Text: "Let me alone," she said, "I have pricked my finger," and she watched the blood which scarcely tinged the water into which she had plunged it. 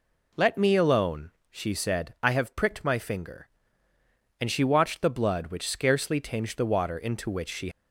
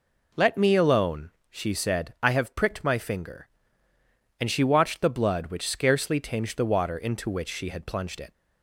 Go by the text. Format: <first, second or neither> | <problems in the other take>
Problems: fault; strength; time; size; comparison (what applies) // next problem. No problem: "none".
second | stops before "had plunged it"; at 7.7 s